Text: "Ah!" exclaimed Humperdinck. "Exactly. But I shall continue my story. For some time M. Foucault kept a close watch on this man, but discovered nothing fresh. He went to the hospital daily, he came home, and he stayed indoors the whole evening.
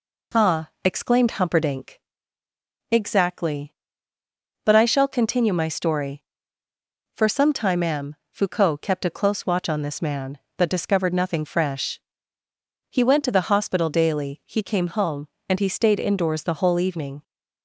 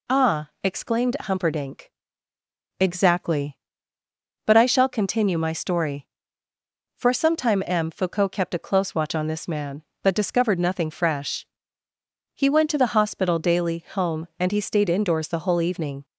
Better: first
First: none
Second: skips "he came"; at 13.8 s

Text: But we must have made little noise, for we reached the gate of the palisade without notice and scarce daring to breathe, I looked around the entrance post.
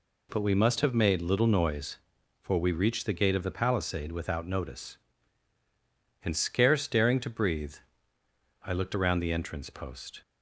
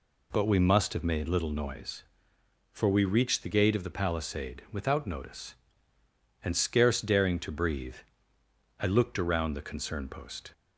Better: first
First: none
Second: says "concern" for "entrance"; at 9.6 s

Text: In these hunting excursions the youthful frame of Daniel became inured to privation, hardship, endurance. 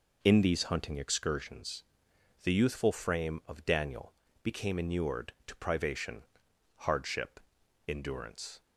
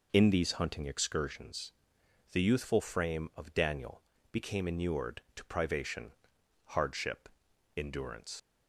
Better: first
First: pauses between "excursions" and "the"; noticeable; at 1.8 s; 0.60 s long // pauses between "Daniel" and "became"; slight; at 4.1 s; 0.30 s long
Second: pauses between "excursions" and "the"; noticeable; at 1.7 s; 0.60 s long // pauses between "Daniel" and "became"; slight; at 4.0 s; 0.30 s long // leaves "endurance" unfinished; at 8.3 s; 95 ms

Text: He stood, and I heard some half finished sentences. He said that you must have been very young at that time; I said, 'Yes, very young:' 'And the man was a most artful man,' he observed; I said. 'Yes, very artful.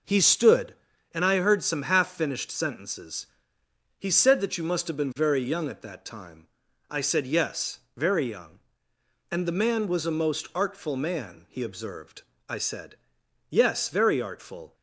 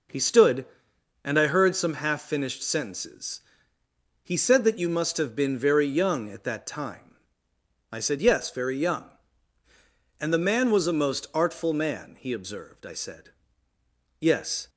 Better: first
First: none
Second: stops before "very artful"; at 14.6 s

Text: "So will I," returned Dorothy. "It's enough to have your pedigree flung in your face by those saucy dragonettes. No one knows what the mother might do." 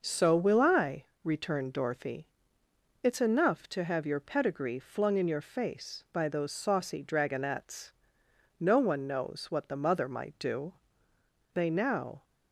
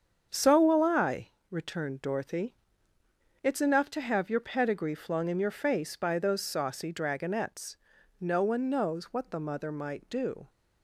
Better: second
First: starts louder than the rest; noticeable; until 1.0 s; 6 dB // goes on to say "They now"; noticeable; from 11.5 s on; 0.70 s long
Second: starts louder than the rest; strong; until 1.3 s; 7.5 dB

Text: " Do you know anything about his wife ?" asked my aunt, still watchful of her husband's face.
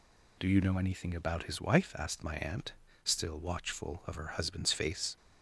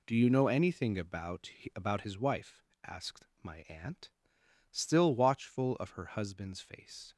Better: first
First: none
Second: says "about" twice; at 1.7 s // pauses between "asked" and "my"; slight; at 3.2 s; 0.16 s long

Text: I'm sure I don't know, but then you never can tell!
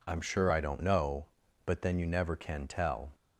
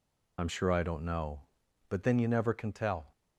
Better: first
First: none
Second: loses the start of "I'm"; at 0.3 s; 50 ms

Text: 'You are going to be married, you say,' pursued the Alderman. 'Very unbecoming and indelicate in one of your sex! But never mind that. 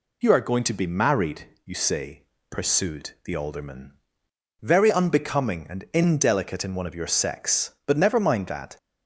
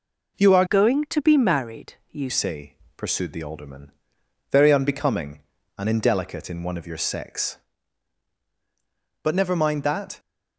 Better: first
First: none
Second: changes voice from "going" to "you"; from 0.6 to 2.3 s; 1.7 s long

